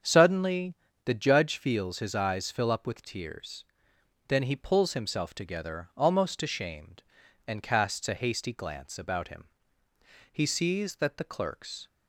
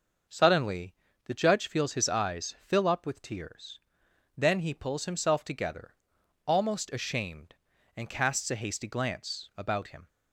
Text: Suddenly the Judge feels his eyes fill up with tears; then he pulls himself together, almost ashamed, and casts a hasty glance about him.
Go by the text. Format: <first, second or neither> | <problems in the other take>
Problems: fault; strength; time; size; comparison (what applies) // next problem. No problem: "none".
second | starts louder than the rest; strong; until 1.3 s; 7.5 dB; also in the second // pauses between "Suddenly" and "the"; slight; at 0.7 s; 0.30 s long; slight in the second // goes on to say "He sees that the clerks"; from 10.3 s on; 1.5 s long